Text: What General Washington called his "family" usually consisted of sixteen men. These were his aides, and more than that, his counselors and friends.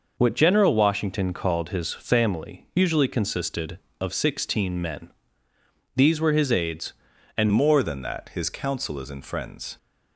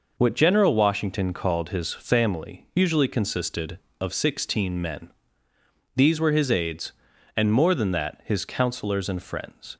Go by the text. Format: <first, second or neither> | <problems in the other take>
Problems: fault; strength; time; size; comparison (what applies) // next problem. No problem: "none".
second | changes voice at "more"; from 7.5 s on; 2.2 s long